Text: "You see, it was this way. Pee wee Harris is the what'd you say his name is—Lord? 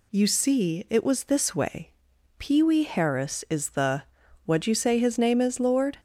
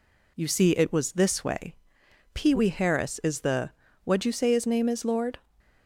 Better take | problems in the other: neither | pauses between "the" and "what'd"; the same in both

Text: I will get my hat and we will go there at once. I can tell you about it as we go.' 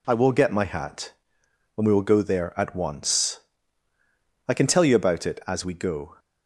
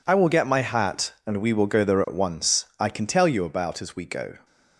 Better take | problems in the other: first | skips "it"; at 3.8 s

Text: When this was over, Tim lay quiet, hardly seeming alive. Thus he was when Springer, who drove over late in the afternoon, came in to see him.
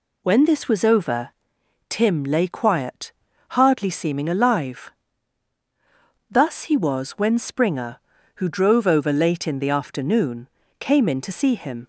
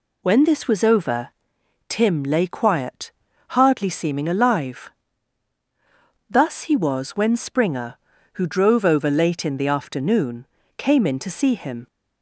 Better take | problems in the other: neither | none

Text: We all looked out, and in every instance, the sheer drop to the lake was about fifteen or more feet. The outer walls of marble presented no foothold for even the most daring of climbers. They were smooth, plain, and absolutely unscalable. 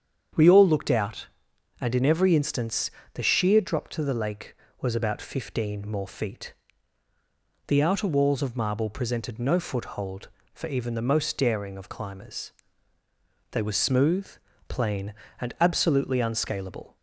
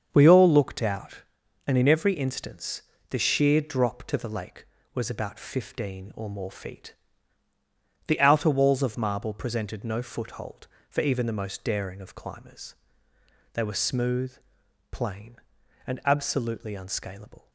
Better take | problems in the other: second | starts louder than the rest; strong; until 1.8 s; 8 dB; strong in the second // skips "or"; at 5.8 s

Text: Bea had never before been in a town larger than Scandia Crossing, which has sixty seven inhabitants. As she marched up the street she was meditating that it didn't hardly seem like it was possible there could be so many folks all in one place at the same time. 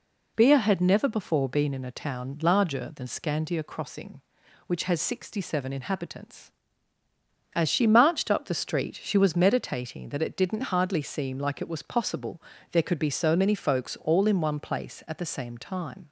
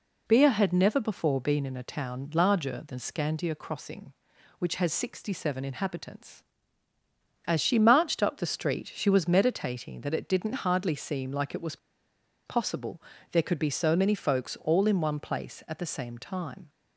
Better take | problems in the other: first | pauses between "was" and "possible"; noticeable; at 11.7 s; 0.69 s long // pauses between "possible" and "there"; slight; at 13.0 s; 0.30 s long; slight in the first

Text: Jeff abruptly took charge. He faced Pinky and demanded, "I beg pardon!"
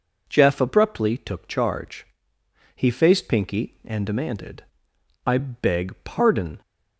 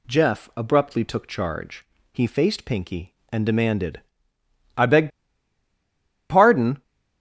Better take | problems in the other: first | pauses between "beg" and "pardon"; at 5.0 s; 1.2 s long

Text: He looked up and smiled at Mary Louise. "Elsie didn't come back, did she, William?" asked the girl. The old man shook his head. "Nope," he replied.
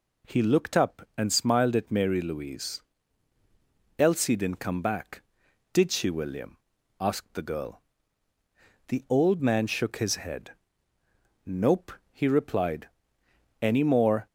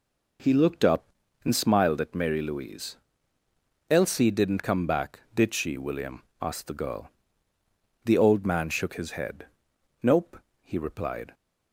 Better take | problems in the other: second | goes on to say "Any more"; noticeable; from 13.6 s on; 0.66 s long

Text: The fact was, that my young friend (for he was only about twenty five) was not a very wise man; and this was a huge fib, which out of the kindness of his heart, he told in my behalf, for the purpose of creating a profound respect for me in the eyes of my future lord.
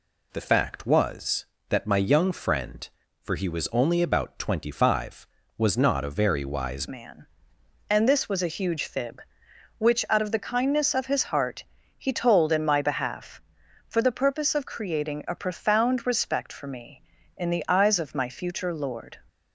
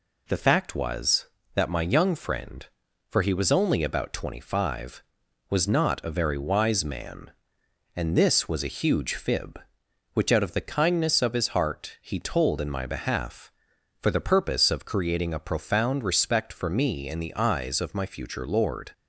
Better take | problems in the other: second | changes voice at "man"; from 6.8 s on; 12.3 s long

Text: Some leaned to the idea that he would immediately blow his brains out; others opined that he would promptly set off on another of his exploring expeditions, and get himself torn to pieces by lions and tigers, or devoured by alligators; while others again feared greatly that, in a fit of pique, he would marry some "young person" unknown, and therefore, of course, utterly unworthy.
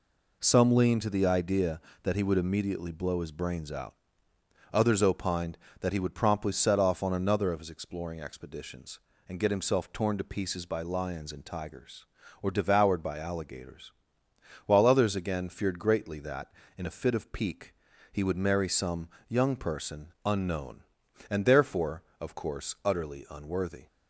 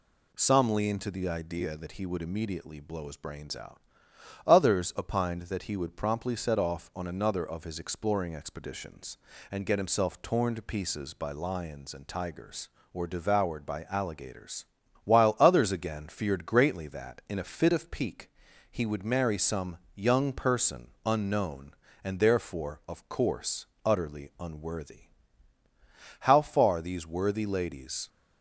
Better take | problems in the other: first | pauses between "some" and "young"; slight; at 19.7 s; 0.18 s long; slight in the first // goes on to say "How far these worthy ladies"; strong; from 26.2 s on; 1.8 s long

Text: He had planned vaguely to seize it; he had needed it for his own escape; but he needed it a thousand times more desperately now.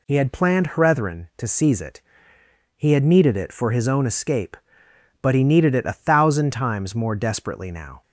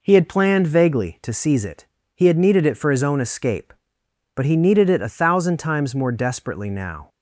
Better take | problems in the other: second | says "hrethren" for "vaguely"; at 0.7 s

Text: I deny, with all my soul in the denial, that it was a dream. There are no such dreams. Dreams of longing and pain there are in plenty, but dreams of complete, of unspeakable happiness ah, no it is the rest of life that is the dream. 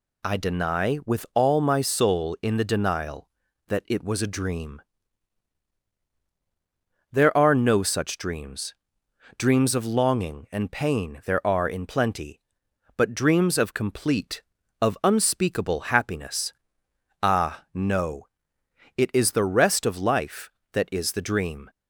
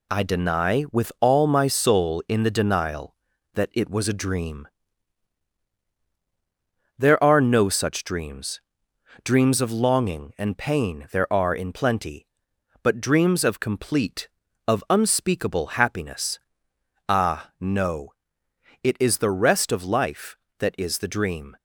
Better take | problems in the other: first | gets quieter; noticeable; throughout; 6 dB // pauses between "happiness" and "ah"; noticeable; at 16.3 s; 0.68 s long; noticeable in the first // pauses between "no" and "it"; noticeable; at 18.0 s; 0.74 s long; noticeable in the first

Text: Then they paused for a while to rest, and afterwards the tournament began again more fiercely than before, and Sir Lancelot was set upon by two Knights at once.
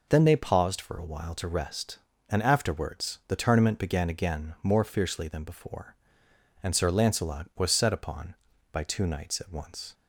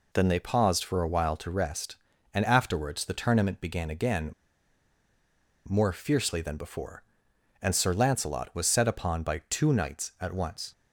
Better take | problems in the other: first | pauses between "again" and "more"; strong; at 4.3 s; 1.3 s long

